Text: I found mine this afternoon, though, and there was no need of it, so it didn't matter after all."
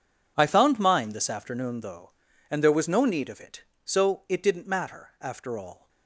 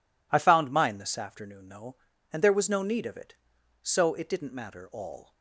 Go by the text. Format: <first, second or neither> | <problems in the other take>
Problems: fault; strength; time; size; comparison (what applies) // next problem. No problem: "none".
first | skips "after"; at 4.8 s